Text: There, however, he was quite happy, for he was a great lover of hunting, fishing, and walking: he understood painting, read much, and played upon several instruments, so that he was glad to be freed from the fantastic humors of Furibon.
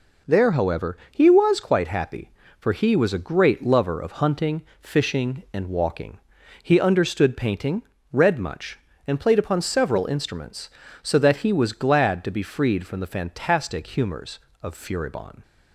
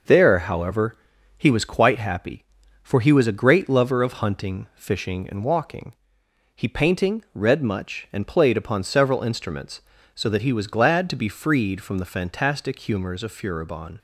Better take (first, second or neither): first